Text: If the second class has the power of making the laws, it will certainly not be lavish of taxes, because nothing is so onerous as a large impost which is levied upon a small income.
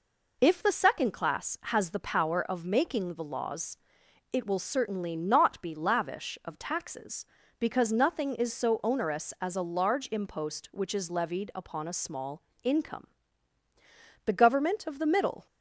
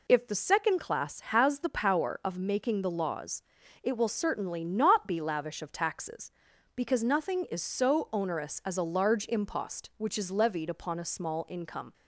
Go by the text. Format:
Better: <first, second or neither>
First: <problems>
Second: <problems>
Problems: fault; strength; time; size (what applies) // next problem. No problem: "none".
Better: second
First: pauses between "small" and "income"; slight; at 12.4 s; 0.22 s long // goes on to say "The government of the middle"; noticeable; from 14.2 s on; 1.2 s long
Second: none